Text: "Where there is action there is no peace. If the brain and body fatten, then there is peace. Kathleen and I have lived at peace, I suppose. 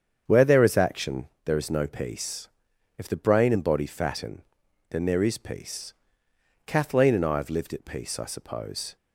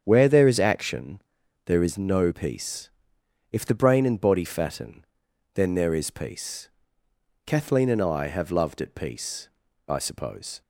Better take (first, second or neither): first